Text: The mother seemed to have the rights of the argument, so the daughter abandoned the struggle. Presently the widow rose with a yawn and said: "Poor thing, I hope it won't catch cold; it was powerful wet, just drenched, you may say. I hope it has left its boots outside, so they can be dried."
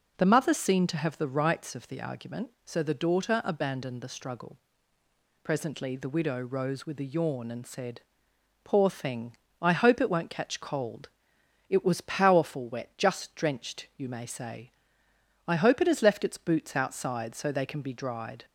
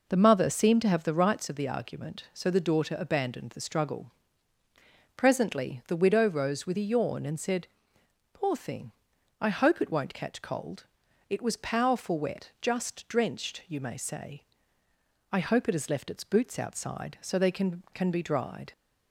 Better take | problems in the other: first | says "can" twice; at 17.9 s

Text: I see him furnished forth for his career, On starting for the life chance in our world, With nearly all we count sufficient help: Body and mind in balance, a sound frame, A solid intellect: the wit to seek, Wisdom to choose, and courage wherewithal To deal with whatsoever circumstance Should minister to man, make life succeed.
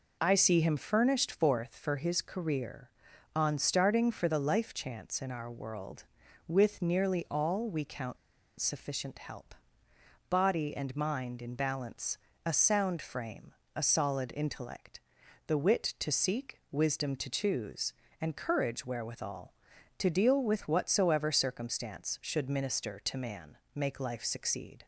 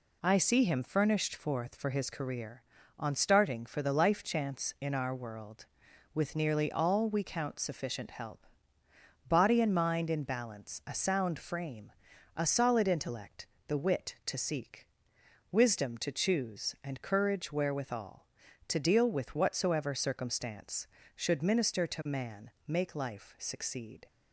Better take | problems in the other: second | pauses between "count" and "sufficient"; at 8.1 s; 0.43 s long

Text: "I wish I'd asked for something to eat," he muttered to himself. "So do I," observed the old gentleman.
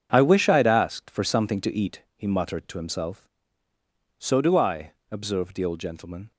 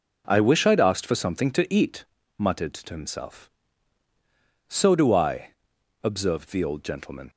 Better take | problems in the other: first | skips "he"; at 2.1 s

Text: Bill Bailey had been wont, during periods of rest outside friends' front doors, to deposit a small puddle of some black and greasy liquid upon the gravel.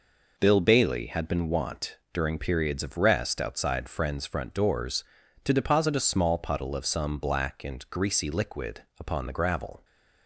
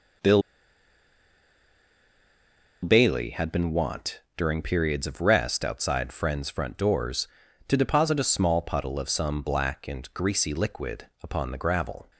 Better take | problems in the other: first | pauses between "Bill" and "Bailey"; strong; at 0.4 s; 2.4 s long // pauses between "liquid" and "upon"; slight; at 11.0 s; 0.16 s long; slight in the first

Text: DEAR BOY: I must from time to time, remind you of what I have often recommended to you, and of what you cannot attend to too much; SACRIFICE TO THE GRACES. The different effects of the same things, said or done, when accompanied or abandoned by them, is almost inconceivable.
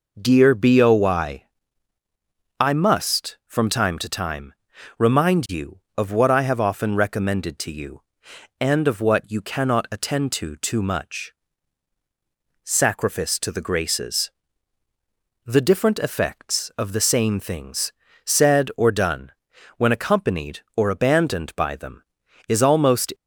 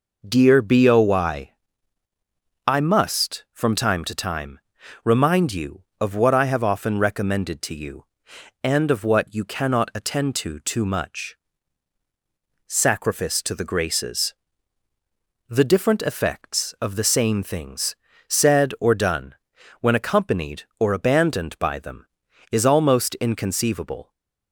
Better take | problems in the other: second | stops before "inconceivable"; at 23.1 s

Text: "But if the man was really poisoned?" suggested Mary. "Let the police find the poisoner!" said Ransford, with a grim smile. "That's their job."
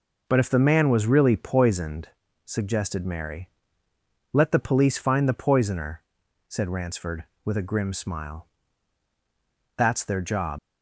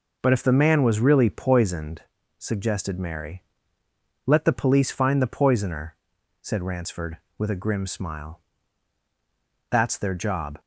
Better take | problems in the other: second | leaves "job" unfinished; at 10.5 s; 75 ms

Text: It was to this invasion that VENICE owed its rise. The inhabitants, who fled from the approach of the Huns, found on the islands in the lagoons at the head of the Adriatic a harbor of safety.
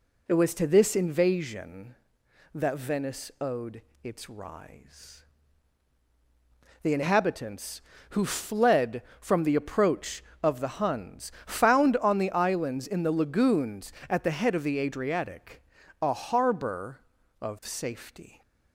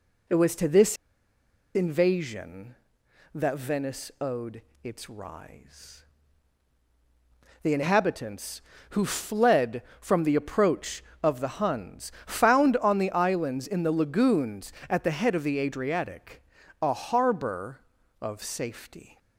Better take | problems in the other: first | pauses between "this" and "invasion"; noticeable; at 0.9 s; 0.79 s long // pauses between "owed" and "its"; slight; at 4.6 s; 0.20 s long; slight in the first // pauses between "Adriatic" and "a"; at 16.4 s; 0.38 s long; also in the first

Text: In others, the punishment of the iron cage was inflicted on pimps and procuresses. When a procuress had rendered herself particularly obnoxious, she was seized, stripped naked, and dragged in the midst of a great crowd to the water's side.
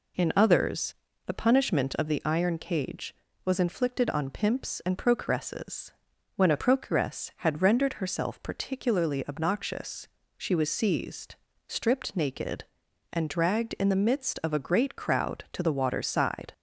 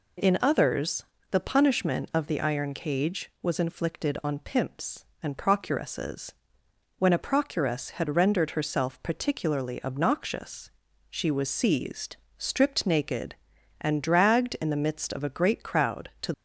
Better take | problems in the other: first | stops before "the water's side"; at 16.3 s

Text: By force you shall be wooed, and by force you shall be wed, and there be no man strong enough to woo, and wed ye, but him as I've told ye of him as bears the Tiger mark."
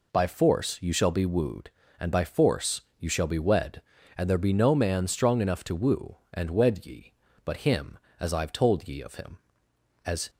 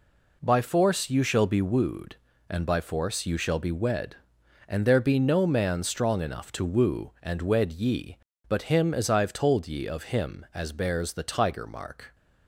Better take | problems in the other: second | pauses between "force" and "you"; slight; at 2.8 s; 0.16 s long // stops before "bears the Tiger mark"; at 10.2 s

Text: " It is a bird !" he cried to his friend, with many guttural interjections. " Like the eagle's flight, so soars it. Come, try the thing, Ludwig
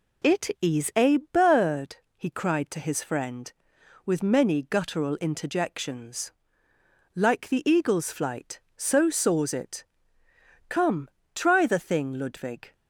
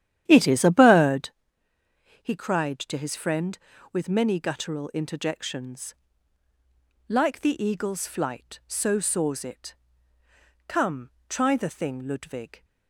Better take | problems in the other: first | starts louder than the rest; strong; until 1.4 s; 11.5 dB

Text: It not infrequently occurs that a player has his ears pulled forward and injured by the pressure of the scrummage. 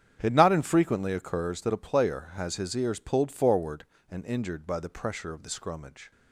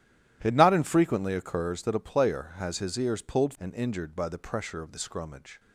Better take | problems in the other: first | starts louder than the rest; strong; until 1.4 s; 13.5 dB; strong in the first // skips "forward"; at 3.5 s

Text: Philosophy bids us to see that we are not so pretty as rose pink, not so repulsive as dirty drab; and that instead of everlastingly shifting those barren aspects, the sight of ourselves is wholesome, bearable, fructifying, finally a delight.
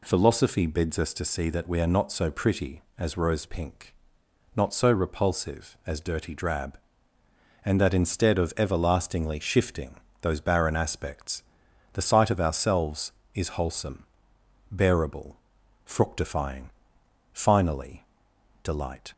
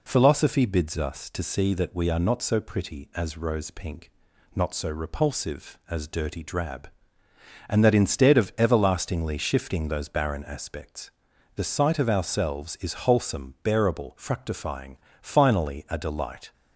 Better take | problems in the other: second | pauses between "shifting" and "those"; slight; at 9.9 s; 0.24 s long // skips "a"; at 18.3 s

